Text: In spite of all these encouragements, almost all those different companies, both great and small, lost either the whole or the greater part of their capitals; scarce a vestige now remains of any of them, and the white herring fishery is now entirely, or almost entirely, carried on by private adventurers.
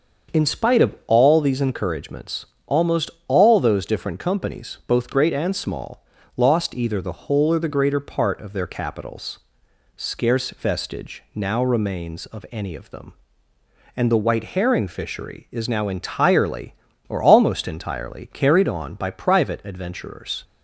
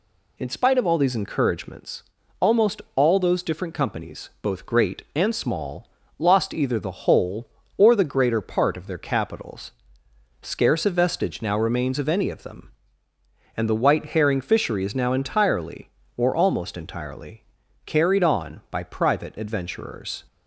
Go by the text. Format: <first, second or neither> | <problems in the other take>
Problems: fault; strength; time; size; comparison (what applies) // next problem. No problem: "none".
second | starts louder than the rest; until 1.4 s; 6.5 dB // pauses between "almost" and "all"; slight; at 3.0 s; 0.16 s long // skips "a"; at 10.5 s